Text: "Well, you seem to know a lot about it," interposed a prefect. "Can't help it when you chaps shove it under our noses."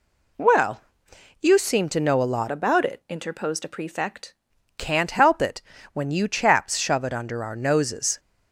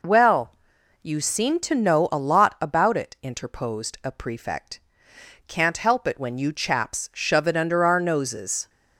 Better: second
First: changes voice from "about" to "prefect"; from 2.5 to 4.3 s; 1.8 s long // pauses between "it" and "when"; slight; at 5.6 s; 0.32 s long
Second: none

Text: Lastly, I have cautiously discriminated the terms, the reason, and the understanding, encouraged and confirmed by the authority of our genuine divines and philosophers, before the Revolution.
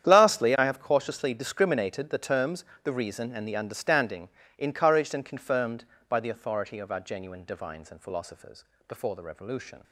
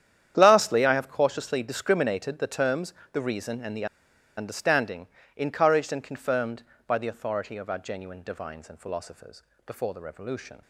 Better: first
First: starts louder than the rest; strong; until 1.1 s; 9.5 dB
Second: starts louder than the rest; strong; until 1.3 s; 9.5 dB // pauses between "the" and "understanding"; noticeable; at 3.8 s; 0.51 s long

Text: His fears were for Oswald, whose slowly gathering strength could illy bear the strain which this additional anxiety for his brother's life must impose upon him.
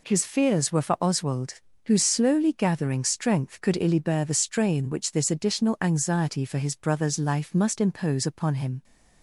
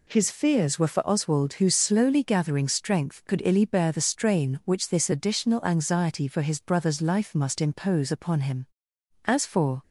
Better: first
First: none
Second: goes on to say "As for"; from 9.2 s on; 0.56 s long

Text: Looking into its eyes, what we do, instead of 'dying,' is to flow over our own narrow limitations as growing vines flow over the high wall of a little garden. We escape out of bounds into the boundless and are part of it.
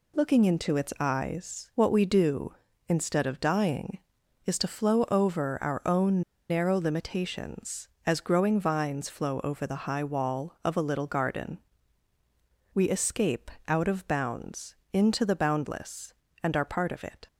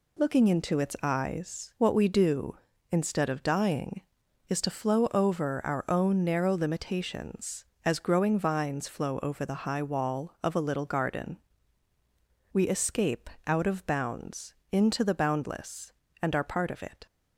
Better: second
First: pauses between "own" and "narrow"; slight; at 6.2 s; 0.29 s long // pauses between "escape" and "out"; slight; at 13.5 s; 0.16 s long // pauses between "bounds" and "into"; slight; at 14.7 s; 0.18 s long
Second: pauses between "escape" and "out"; slight; at 13.2 s; 0.16 s long // pauses between "bounds" and "into"; slight; at 14.5 s; 0.18 s long

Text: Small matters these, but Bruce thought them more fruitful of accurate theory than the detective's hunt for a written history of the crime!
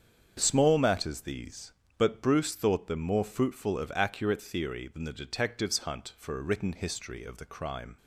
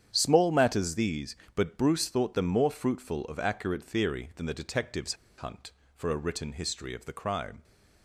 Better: first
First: starts louder than the rest; strong; until 1.3 s; 7 dB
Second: starts louder than the rest; strong; until 1.1 s; 8.5 dB // pauses between "detective's" and "hunt"; slight; at 5.1 s; 0.24 s long

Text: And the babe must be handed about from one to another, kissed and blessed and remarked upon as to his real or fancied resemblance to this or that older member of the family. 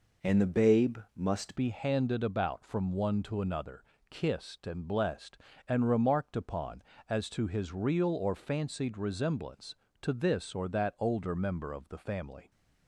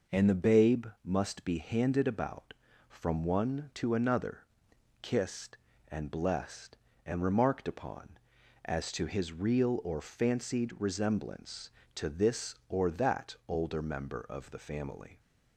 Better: second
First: pauses between "babe" and "must"; slight; at 0.9 s; 0.18 s long // changes voice at "be"; from 1.5 s on; 10.9 s long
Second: pauses between "babe" and "must"; slight; at 0.8 s; 0.18 s long

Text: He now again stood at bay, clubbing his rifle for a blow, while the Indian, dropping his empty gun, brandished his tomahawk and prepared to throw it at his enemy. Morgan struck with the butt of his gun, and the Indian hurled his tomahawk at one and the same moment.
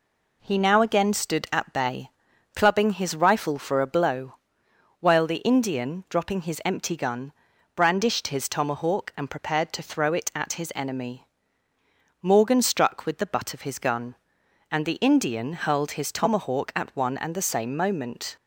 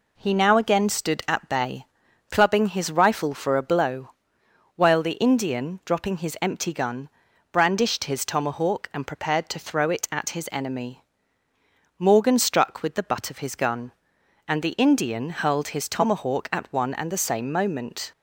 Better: neither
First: none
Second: none

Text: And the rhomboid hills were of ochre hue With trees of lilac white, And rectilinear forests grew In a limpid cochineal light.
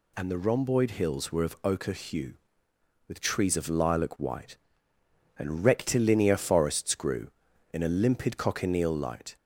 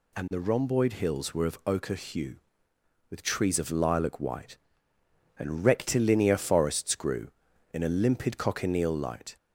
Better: neither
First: none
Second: none

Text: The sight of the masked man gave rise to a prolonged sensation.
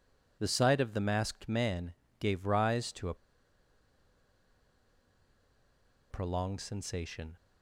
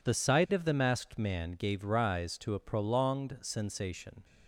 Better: second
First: pauses between "man" and "gave"; slight; at 1.9 s; 0.26 s long // pauses between "a" and "prolonged"; strong; at 3.1 s; 2.9 s long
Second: none

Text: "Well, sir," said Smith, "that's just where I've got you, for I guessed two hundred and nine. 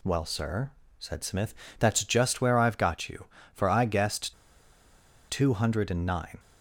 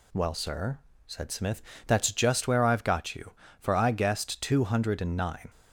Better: second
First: pauses between "guessed" and "two"; noticeable; at 4.3 s; 0.95 s long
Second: none

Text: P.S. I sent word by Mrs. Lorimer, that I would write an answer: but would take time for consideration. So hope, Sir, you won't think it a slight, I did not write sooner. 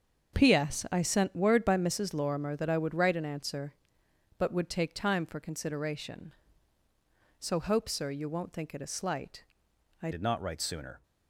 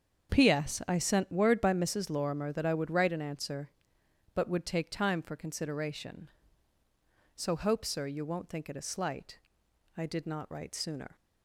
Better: second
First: starts louder than the rest; until 1.4 s; 6.5 dB // changes voice at "did"; from 10.1 s on; 0.9 s long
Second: starts louder than the rest; strong; until 1.3 s; 7 dB

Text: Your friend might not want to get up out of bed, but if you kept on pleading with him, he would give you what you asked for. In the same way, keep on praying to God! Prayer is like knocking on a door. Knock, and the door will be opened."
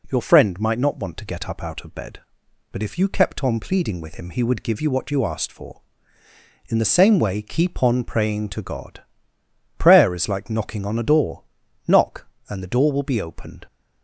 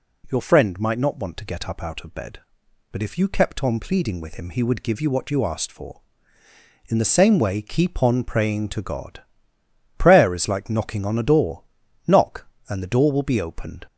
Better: first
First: none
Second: gets louder; slight; throughout; 2 dB

